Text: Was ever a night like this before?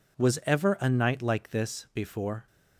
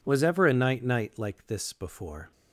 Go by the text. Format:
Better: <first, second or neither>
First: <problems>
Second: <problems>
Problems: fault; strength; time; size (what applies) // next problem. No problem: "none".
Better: first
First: none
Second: says "night" twice; at 0.8 s